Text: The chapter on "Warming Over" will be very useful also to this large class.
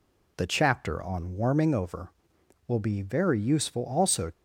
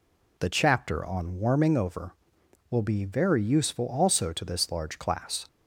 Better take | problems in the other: second | stops before "to this large class"; at 4.3 s

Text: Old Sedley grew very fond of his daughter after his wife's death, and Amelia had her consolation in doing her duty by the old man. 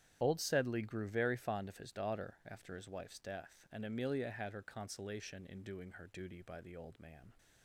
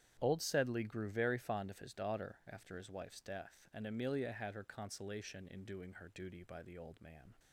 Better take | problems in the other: second | loses the start of "Old"; at 0.2 s; 35 ms // starts louder than the rest; strong; until 1.2 s; 10.5 dB; strong in the second

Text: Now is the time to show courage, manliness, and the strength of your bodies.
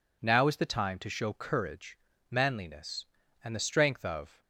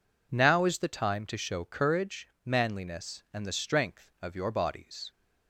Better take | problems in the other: second | stops before "your bodies"; at 4.4 s

